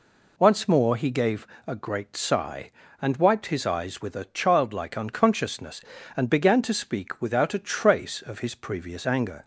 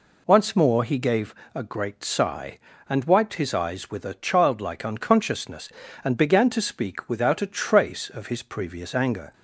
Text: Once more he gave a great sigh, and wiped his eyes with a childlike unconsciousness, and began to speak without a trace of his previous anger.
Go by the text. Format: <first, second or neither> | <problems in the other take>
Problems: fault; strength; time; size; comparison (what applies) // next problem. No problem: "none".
neither | pauses between "gave" and "a"; slight; the same in both